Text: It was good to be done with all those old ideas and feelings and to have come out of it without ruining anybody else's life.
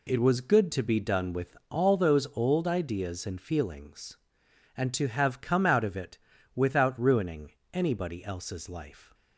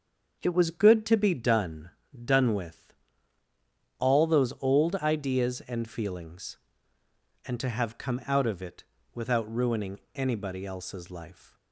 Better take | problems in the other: first | starts louder than the rest; until 1.4 s; 7 dB // says "done" twice; at 2.2 s // pauses between "with" and "all"; at 2.9 s; 1.0 s long // pauses between "it" and "without"; slight; at 8.8 s; 0.32 s long; also in the first // pauses between "ruining" and "anybody"; slight; at 9.9 s; 0.16 s long; slight in the first

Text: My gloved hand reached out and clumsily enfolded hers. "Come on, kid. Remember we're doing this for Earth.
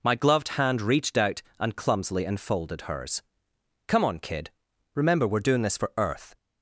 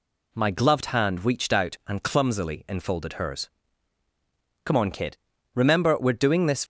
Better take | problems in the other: first | stops before "for Earth"; at 6.6 s

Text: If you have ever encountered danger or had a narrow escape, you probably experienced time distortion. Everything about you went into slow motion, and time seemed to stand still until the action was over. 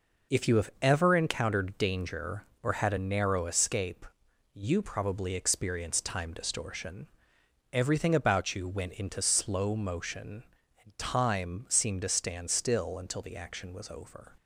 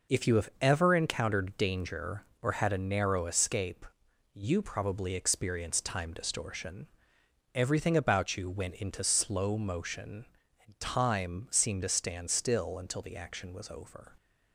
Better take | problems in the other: neither | none

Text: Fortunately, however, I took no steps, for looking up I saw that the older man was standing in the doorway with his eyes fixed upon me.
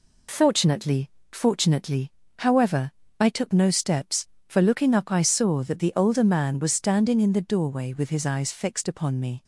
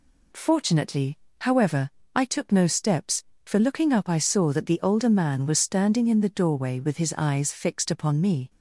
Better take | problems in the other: second | says "Fortunately" twice; at 1.3 s

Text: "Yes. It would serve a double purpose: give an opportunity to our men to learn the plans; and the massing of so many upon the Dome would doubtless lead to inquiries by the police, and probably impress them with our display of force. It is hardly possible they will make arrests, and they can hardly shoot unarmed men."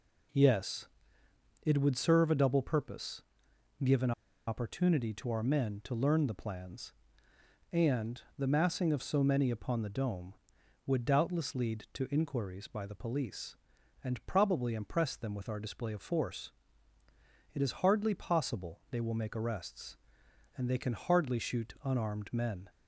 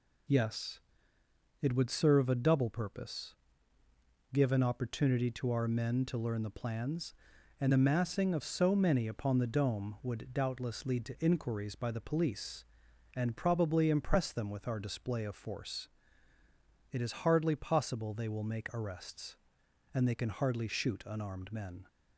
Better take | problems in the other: second | pauses between "an" and "opportunity"; at 4.1 s; 0.36 s long // pauses between "and" and "the"; slight; at 8.2 s; 0.16 s long

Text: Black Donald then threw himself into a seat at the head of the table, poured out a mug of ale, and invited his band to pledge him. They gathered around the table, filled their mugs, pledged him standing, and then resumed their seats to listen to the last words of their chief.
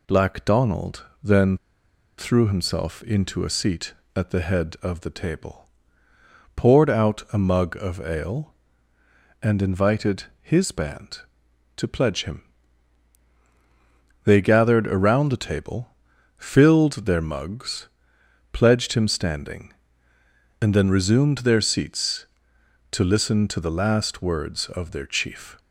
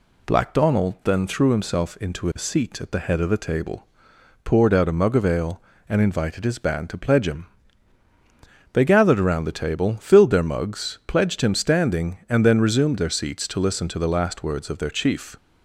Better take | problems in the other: second | pauses between "Donald" and "then"; slight; at 1.0 s; 0.16 s long // pauses between "then" and "threw"; noticeable; at 1.5 s; 0.61 s long // pauses between "invited" and "his"; slight; at 10.2 s; 0.18 s long

